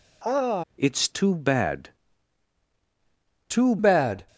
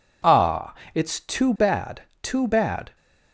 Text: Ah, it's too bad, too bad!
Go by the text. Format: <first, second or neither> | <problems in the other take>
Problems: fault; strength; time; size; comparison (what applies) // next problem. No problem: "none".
second | changes voice from "it's" to "too"; from 0.7 to 3.7 s; 3.0 s long